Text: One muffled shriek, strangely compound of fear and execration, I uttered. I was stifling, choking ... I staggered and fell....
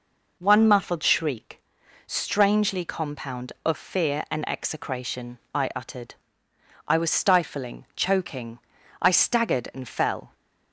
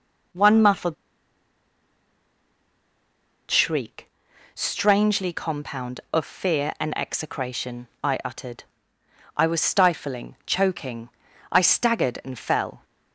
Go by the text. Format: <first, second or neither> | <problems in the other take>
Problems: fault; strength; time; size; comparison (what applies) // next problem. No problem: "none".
first | pauses between "muffled" and "shriek"; strong; at 0.9 s; 2.5 s long